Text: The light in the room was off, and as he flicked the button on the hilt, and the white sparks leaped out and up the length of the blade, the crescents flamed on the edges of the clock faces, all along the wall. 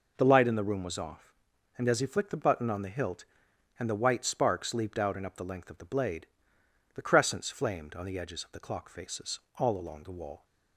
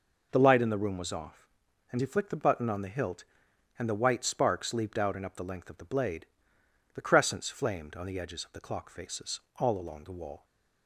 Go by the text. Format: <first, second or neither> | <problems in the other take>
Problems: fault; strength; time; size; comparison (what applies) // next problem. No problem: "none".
first | skips "as"; at 1.9 s